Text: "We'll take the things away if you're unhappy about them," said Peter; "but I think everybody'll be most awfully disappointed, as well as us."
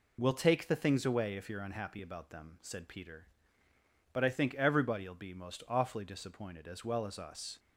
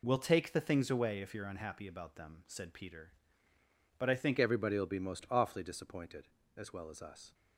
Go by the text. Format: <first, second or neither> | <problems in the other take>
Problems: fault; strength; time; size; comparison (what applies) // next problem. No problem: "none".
first | changes voice at "everybody'll"; from 4.3 s on; 3.0 s long